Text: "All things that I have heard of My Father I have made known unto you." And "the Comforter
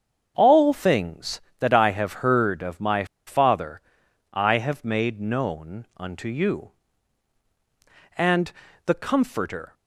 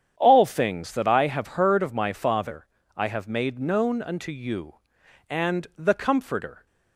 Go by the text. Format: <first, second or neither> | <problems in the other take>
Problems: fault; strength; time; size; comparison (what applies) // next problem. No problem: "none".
second | starts louder than the rest; strong; until 1.3 s; 7.5 dB; strong in the second // pauses between "My" and "Father"; slight; at 3.0 s; 0.20 s long // pauses between "Father" and "I"; noticeable; at 3.8 s; 0.50 s long; slight in the second // pauses between "And" and "the"; slight; at 8.5 s; 0.32 s long